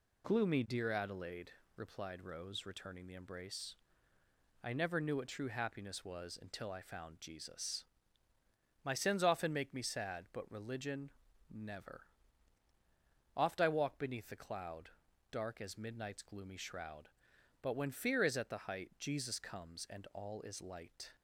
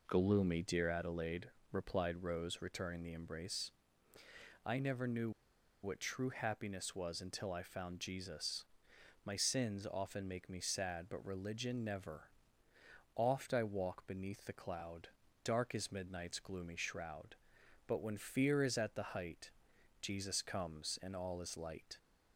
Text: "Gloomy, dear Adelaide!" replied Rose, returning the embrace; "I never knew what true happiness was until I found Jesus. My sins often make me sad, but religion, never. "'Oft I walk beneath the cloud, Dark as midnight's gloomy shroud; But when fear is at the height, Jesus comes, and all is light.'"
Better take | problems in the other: first | pauses between "knew" and "what"; noticeable; at 5.3 s; 0.52 s long

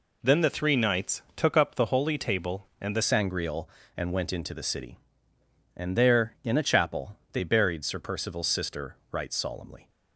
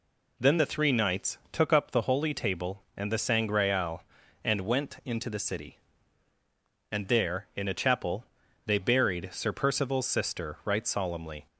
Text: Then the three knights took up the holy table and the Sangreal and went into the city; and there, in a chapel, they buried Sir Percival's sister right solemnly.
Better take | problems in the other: second | changes voice at "Sangreal"; from 3.0 s on; 6.8 s long

